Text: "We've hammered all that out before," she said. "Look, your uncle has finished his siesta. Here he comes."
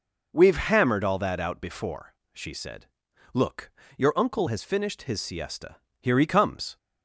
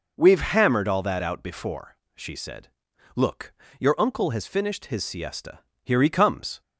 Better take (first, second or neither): neither